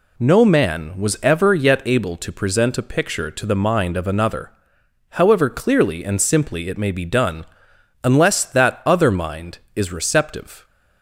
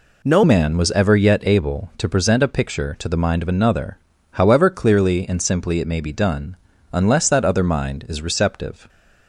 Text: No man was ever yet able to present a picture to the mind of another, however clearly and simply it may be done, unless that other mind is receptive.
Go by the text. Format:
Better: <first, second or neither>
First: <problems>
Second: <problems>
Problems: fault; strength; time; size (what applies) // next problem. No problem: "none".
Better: first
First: none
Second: changes voice at "man"; from 0.4 s on; 8.4 s long